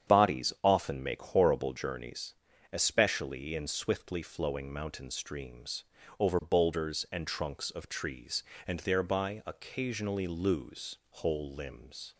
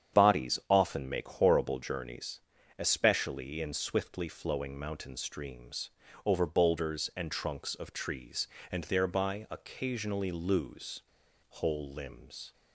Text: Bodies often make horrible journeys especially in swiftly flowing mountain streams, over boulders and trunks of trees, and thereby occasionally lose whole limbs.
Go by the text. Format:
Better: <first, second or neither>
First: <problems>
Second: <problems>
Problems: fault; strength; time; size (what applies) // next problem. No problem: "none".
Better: first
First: starts louder than the rest; strong; until 1.1 s; 8.5 dB // pauses between "journeys" and "especially"; at 2.3 s; 0.38 s long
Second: starts louder than the rest; strong; until 1.2 s; 8.5 dB // pauses between "journeys" and "especially"; at 2.3 s; 0.38 s long // pauses between "lose" and "whole"; noticeable; at 11.0 s; 0.46 s long